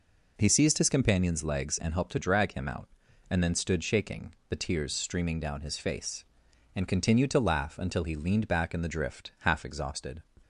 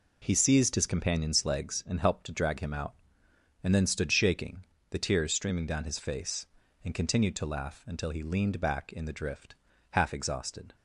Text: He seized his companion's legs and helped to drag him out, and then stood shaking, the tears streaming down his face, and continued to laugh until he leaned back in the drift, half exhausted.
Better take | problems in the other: neither | none

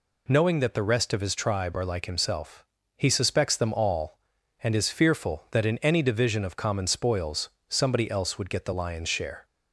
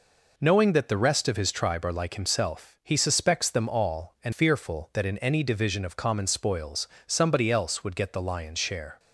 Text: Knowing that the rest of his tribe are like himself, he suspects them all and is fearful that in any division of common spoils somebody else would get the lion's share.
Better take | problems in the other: first | skips "is"; at 4.3 s // pauses between "spoils" and "somebody"; slight; at 6.8 s; 0.18 s long; slight in the first

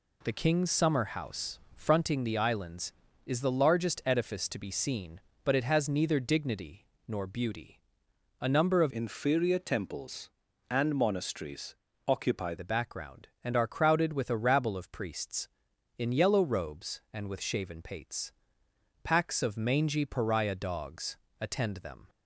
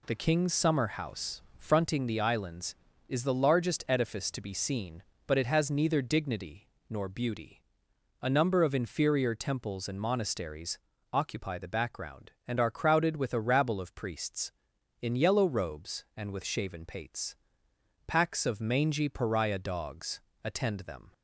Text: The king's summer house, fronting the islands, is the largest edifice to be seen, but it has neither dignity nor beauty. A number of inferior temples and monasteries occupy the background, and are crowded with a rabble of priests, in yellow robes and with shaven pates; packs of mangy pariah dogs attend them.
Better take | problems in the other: second | pauses between "dignity" and "nor"; slight; at 6.8 s; 0.22 s long; slight in the second // changes voice from "inferior" to "occupy"; from 8.9 to 12.5 s; 3.6 s long // pauses between "monasteries" and "occupy"; slight; at 11.7 s; 0.28 s long; slight in the second // pauses between "dogs" and "attend"; slight; at 21.1 s; 0.24 s long; slight in the second

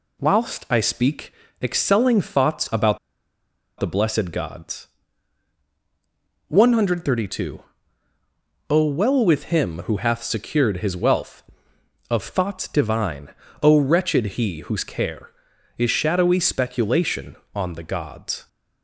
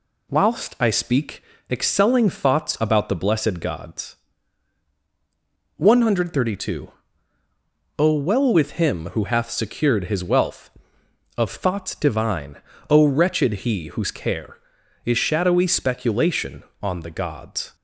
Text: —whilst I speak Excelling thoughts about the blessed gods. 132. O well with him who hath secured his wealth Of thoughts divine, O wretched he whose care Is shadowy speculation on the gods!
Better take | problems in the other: second | pauses between "speak" and "Excelling"; slight; at 1.3 s; 0.28 s long; slight in the second // pauses between "about" and "the"; noticeable; at 2.9 s; 0.81 s long

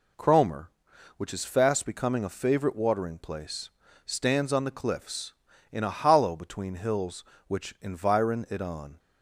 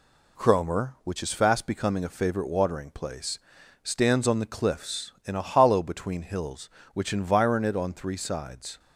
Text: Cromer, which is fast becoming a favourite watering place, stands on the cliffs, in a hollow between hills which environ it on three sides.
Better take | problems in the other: second | stops before "three sides"; at 8.9 s

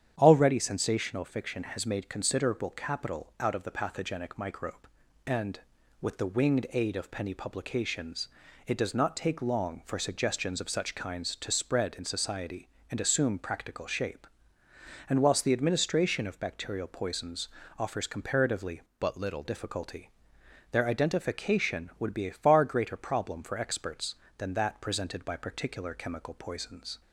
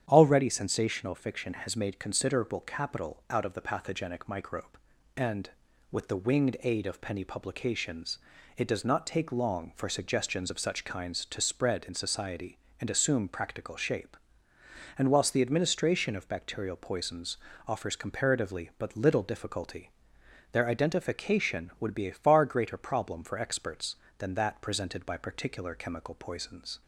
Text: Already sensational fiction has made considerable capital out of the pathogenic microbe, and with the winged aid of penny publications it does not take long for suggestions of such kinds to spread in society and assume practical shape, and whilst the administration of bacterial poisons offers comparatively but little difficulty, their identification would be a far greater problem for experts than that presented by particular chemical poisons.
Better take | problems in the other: second | starts louder than the rest; strong; until 1.1 s; 9 dB; strong in the second // pauses between "publications" and "it"; at 8.2 s; 0.40 s long; also in the second // pauses between "poisons" and "offers"; slight; at 17.4 s; 0.28 s long; slight in the second // changes voice from "but" to "little"; from 18.9 to 19.4 s; 0.5 s long

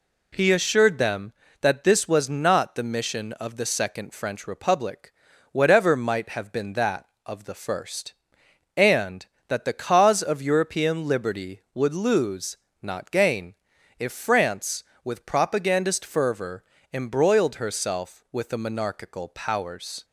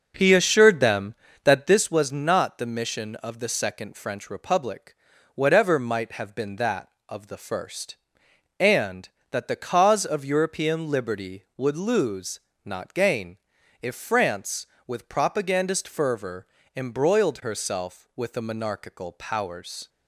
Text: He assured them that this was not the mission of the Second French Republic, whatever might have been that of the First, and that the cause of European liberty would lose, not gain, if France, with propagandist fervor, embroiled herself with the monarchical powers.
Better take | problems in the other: first | starts louder than the rest; noticeable; until 1.8 s; 6 dB

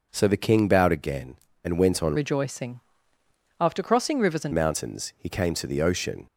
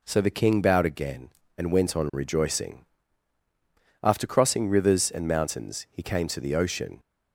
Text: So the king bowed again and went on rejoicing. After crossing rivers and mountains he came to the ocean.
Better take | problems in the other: second | changes voice from "rejoicing" to "and"; from 2.1 to 4.5 s; 2.4 s long

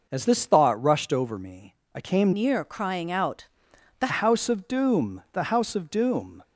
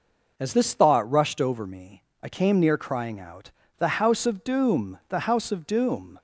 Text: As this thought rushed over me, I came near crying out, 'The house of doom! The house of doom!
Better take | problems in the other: second | changes voice from "near" to "The"; from 2.3 to 4.0 s; 1.7 s long

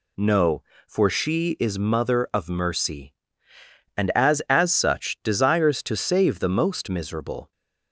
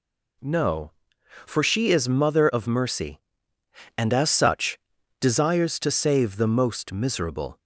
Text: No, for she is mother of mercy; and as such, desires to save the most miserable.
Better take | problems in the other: second | says "as" twice; at 4.4 s

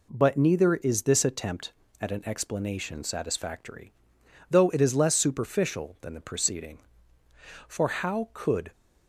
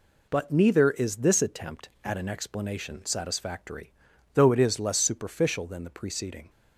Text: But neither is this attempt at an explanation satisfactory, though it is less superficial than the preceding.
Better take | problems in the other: second | goes on to say "For how could"; noticeable; from 7.6 s on; 1.0 s long

